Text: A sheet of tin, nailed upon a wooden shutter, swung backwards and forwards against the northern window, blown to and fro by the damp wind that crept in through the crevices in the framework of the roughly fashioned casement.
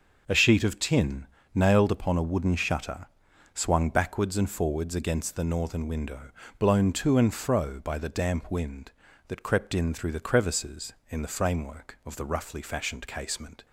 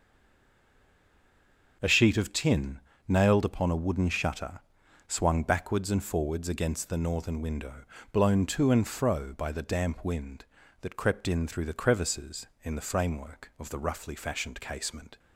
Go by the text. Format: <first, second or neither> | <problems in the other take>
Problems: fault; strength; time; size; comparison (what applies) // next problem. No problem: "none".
first | stays silent before the first word; noticeable; until 1.8 s; 1.8 s long // starts louder than the rest; until 2.8 s; 6 dB; also in the first